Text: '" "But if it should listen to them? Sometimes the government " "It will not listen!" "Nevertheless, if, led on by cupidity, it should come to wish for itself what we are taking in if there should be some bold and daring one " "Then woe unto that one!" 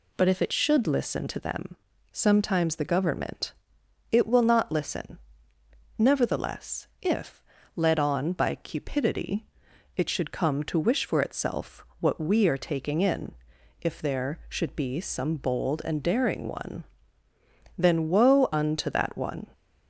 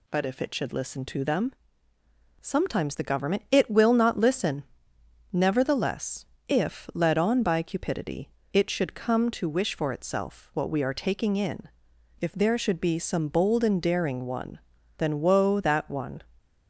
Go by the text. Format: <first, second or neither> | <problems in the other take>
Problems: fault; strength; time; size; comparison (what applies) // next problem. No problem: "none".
first | pauses between "in" and "if"; noticeable; at 11.6 s; 0.54 s long; noticeable in the first // skips "unto"; at 15.5 s